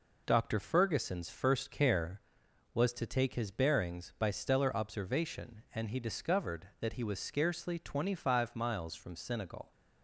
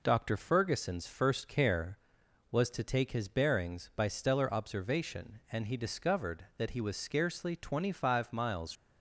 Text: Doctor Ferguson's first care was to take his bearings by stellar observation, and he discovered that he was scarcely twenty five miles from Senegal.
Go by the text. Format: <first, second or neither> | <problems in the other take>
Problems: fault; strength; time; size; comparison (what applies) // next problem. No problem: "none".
first | stops before "from Senegal"; at 8.7 s